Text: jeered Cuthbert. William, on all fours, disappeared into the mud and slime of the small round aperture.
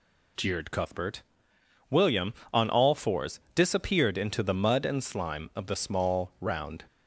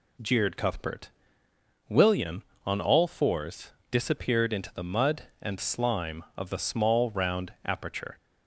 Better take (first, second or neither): second